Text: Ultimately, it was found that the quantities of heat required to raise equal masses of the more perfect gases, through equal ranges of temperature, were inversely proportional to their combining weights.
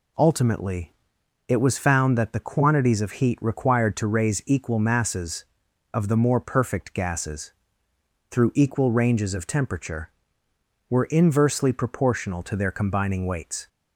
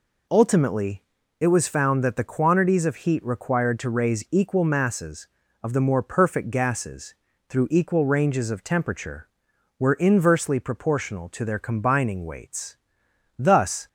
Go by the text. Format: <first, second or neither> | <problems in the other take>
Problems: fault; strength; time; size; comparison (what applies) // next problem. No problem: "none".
first | goes on to say "Thus"; from 13.3 s on; 0.50 s long